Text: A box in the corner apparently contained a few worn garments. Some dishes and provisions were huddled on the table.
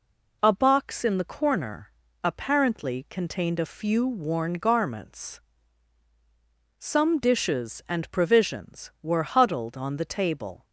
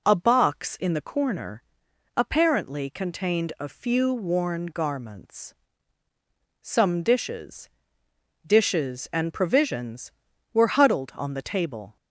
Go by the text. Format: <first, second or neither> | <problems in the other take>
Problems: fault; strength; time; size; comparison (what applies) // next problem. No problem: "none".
first | pauses between "corner" and "apparently"; noticeable; at 1.6 s; 0.54 s long; slight in the first // says "dishes" twice; at 8.4 s